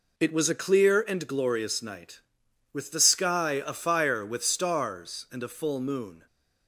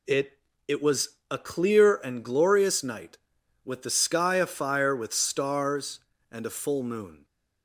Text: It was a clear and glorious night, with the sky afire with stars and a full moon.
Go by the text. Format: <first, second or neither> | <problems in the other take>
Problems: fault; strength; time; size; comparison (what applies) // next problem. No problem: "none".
first | says "It" twice; at 0.6 s